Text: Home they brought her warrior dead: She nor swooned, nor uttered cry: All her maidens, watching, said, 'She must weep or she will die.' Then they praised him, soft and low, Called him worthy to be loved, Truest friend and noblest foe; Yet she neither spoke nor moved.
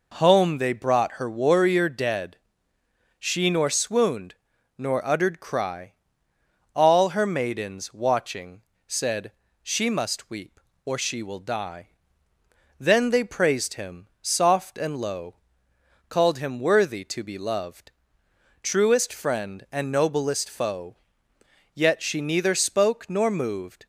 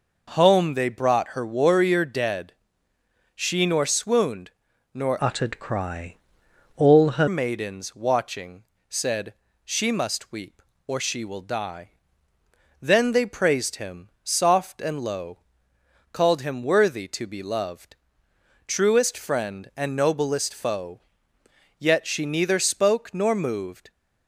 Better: first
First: none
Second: changes voice from "uttered" to "her"; from 5.1 to 7.2 s; 2.1 s long

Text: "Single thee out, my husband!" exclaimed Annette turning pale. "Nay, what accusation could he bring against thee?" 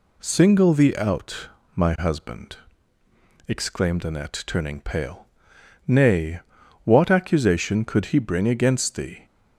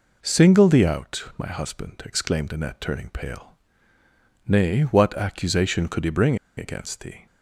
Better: first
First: none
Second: pauses between "bring" and "against"; slight; at 6.3 s; 0.20 s long

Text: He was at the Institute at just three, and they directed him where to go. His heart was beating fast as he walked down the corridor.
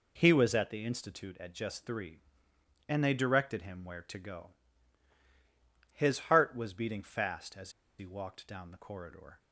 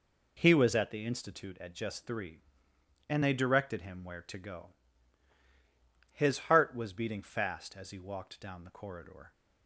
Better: second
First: pauses between "as" and "he"; slight; at 7.7 s; 0.28 s long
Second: none

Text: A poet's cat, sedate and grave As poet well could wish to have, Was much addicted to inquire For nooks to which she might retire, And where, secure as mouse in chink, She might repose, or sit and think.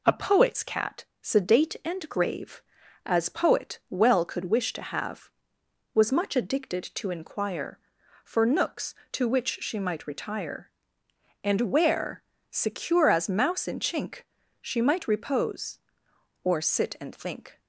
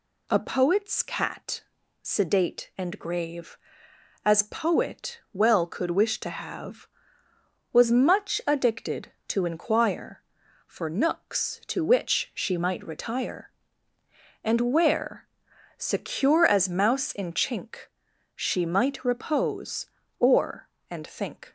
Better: first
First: none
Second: skips "sit"; at 20.7 s

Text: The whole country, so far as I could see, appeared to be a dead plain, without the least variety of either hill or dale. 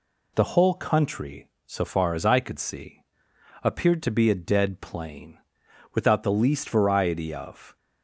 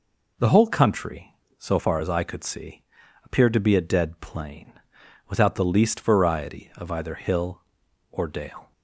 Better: second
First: stops before "either hill or dale"; at 7.7 s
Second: none

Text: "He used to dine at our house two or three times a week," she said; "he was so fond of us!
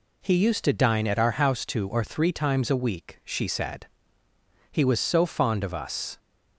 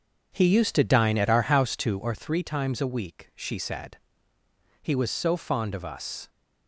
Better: first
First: none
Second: starts louder than the rest; strong; until 2.1 s; 7.5 dB

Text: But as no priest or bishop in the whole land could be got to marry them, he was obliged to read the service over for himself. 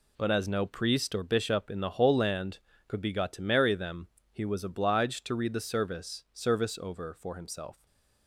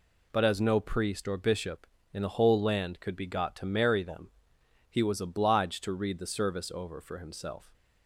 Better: second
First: says "service" twice; at 6.3 s // stays silent after the last word; slight; from 7.7 s on; 0.5 s long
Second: none

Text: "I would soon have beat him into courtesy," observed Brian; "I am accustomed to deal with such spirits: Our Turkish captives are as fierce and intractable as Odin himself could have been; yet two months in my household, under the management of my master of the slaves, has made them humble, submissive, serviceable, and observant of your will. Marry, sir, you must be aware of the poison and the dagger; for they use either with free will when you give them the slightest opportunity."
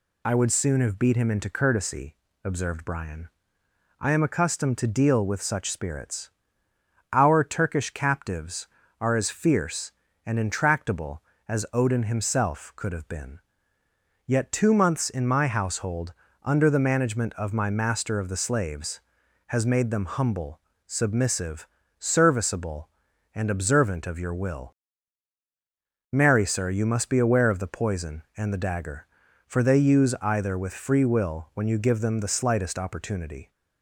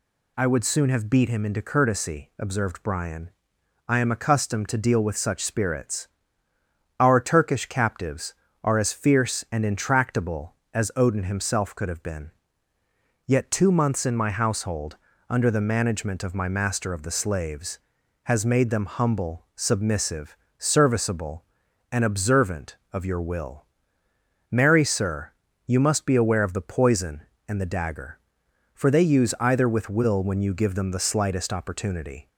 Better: first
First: none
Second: skips "free"; at 29.8 s

